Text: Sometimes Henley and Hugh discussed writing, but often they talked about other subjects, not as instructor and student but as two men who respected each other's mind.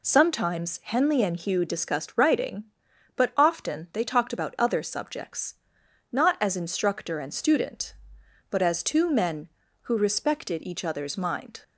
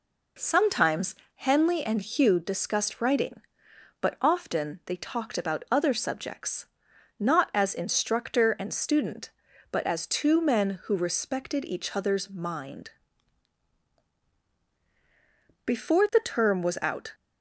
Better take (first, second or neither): first